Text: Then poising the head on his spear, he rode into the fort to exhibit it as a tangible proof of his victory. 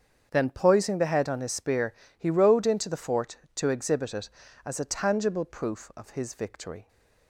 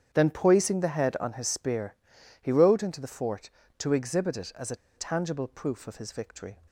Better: first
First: starts louder than the rest; strong; until 1.3 s; 7.5 dB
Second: starts louder than the rest; strong; until 1.1 s; 9 dB // pauses between "a" and "tangible"; slight; at 4.7 s; 0.19 s long

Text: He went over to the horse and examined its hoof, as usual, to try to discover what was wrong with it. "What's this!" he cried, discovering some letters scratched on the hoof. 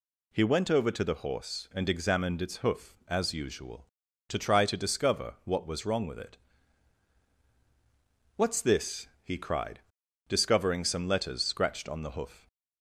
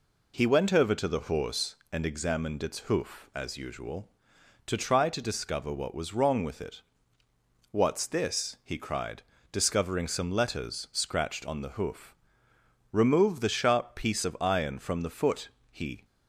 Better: first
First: none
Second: goes on to say "Remove the sharp piece of iron from the foot he"; strong; from 12.9 s on; 3.1 s long

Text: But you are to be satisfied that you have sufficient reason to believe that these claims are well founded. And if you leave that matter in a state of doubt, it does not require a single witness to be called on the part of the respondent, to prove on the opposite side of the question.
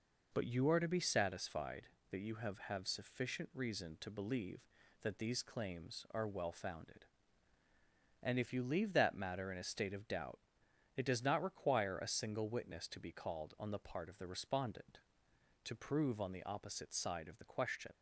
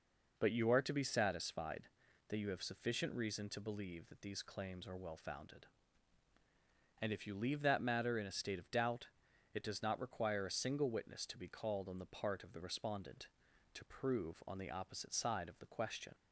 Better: second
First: says "have" twice; at 2.6 s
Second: none

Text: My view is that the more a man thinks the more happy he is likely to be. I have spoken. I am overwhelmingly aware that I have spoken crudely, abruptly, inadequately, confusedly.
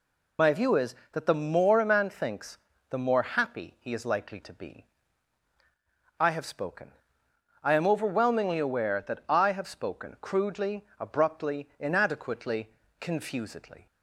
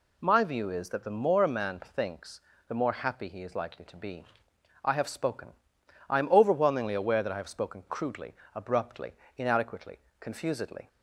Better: second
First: loses the start of "My"; at 0.3 s; 30 ms // pauses between "thinks" and "the"; slight; at 2.5 s; 0.32 s long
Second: pauses between "thinks" and "the"; slight; at 2.4 s; 0.28 s long

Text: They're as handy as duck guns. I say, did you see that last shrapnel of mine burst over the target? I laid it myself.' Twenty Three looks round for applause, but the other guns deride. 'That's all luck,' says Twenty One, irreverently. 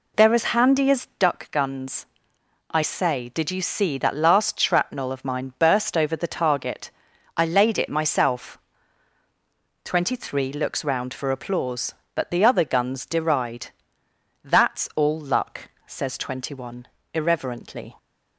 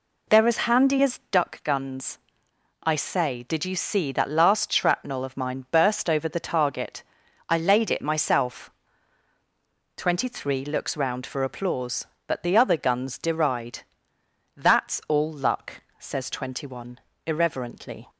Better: neither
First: none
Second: none

